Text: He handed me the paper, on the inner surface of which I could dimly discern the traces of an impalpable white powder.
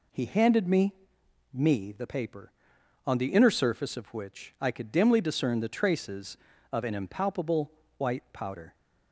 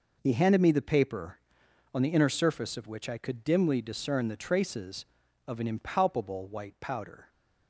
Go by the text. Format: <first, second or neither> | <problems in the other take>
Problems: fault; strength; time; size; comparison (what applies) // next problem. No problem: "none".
second | says "me" twice; at 1.5 s // pauses between "impalpable" and "white"; slight; at 7.7 s; 0.24 s long